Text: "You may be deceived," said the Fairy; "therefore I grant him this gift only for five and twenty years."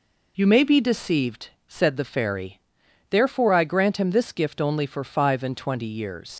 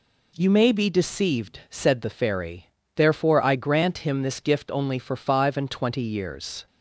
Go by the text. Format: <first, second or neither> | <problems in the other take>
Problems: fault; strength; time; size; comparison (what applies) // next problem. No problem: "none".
second | leaves "years" unfinished; at 6.3 s; 105 ms